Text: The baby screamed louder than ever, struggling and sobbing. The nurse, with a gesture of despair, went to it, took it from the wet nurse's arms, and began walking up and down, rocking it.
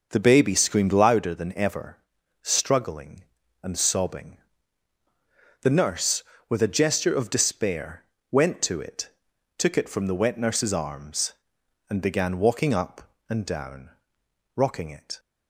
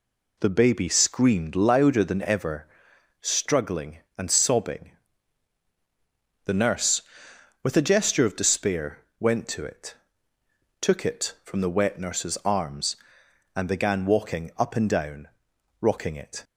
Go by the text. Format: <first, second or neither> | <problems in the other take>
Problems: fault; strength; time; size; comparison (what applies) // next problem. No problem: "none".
second | starts louder than the rest; noticeable; until 1.4 s; 6 dB